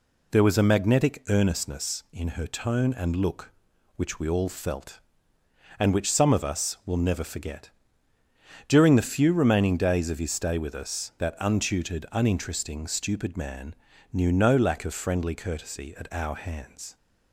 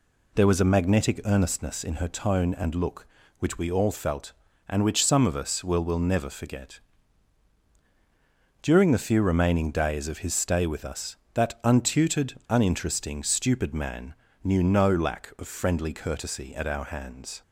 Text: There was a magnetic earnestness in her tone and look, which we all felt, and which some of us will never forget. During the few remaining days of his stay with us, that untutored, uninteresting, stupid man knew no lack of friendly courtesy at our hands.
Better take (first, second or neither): first